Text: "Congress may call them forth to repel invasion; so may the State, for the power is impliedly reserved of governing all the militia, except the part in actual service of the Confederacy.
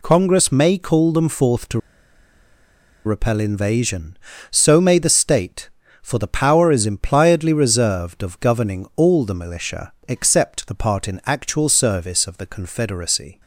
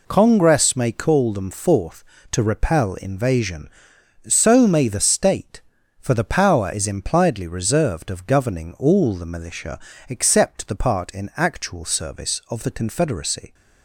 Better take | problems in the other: second | pauses between "to" and "repel"; strong; at 1.7 s; 1.2 s long

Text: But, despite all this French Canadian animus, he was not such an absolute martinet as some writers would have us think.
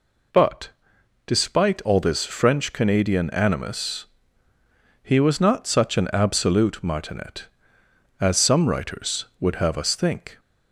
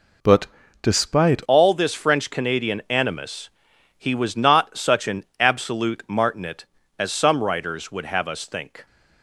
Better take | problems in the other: first | changes voice at "all"; from 1.4 s on; 7.4 s long // pauses between "an" and "absolute"; slight; at 5.2 s; 0.16 s long

